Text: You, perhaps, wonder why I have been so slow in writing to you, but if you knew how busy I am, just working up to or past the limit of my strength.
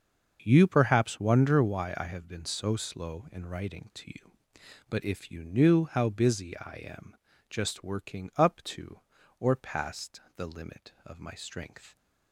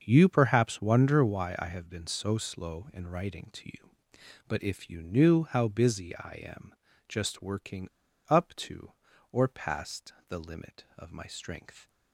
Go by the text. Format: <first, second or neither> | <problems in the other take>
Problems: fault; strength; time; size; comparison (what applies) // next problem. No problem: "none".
first | starts louder than the rest; until 1.0 s; 6.5 dB; also in the first // pauses between "working" and "up"; at 7.8 s; 0.39 s long // pauses between "past" and "the"; slight; at 10.1 s; 0.16 s long; slight in the first